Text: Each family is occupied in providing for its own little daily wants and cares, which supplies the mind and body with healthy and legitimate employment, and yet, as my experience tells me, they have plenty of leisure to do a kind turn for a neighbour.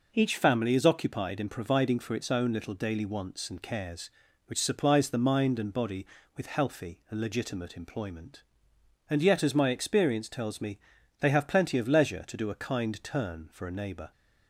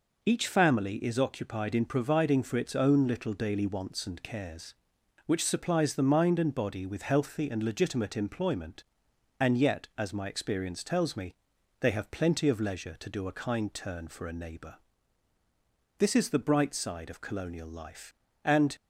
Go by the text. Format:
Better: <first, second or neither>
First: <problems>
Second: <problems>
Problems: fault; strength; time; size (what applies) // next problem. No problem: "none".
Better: first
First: none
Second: goes on to say "This is the bright side of colonial life and"; strong; from 15.9 s on; 2.8 s long